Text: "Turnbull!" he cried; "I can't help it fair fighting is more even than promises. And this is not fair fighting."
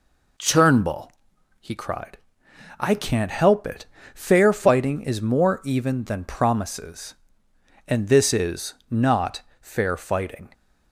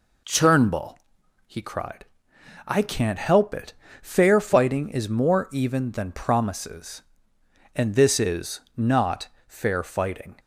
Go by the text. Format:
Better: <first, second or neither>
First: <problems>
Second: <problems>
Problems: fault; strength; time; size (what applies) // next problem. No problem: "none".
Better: neither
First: pauses between "it" and "fair"; slight; at 3.8 s; 0.28 s long // pauses between "is" and "not"; slight; at 8.7 s; 0.16 s long // pauses between "not" and "fair"; slight; at 9.3 s; 0.22 s long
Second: pauses between "it" and "fair"; slight; at 3.7 s; 0.28 s long // pauses between "is" and "not"; slight; at 8.6 s; 0.16 s long // pauses between "not" and "fair"; slight; at 9.2 s; 0.22 s long